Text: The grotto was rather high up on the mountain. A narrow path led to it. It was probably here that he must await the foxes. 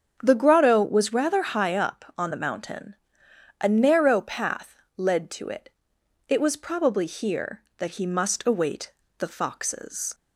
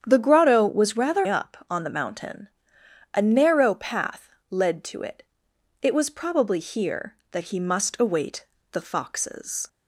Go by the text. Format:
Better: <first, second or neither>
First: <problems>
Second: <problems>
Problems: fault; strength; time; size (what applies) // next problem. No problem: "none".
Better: first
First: starts louder than the rest; strong; until 1.2 s; 7.5 dB // pauses between "path" and "led"; slight; at 4.7 s; 0.20 s long // pauses between "await" and "the"; slight; at 8.9 s; 0.26 s long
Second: starts louder than the rest; strong; until 1.0 s; 8.5 dB // skips "high"; at 1.2 s // pauses between "path" and "led"; slight; at 4.2 s; 0.20 s long // pauses between "await" and "the"; slight; at 8.4 s; 0.26 s long